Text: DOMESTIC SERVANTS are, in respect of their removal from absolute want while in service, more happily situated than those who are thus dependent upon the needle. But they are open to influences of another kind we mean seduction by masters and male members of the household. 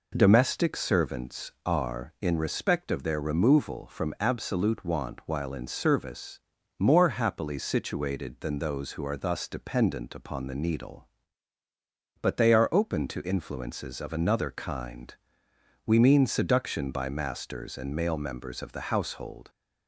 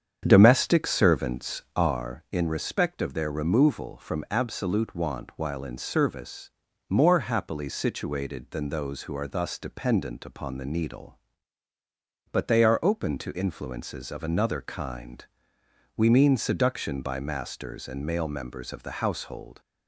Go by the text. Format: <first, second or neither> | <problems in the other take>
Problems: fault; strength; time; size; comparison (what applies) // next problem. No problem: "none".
first | starts louder than the rest; strong; until 2.0 s; 8 dB // pauses between "kind" and "we"; noticeable; at 15.2 s; 0.74 s long; noticeable in the first